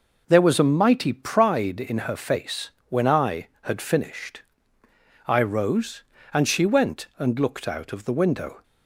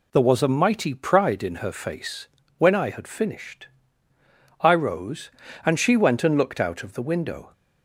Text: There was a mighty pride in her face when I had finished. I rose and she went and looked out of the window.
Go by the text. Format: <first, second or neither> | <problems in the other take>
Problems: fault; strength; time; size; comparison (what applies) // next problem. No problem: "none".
neither | pauses between "face" and "when"; slight; the same in both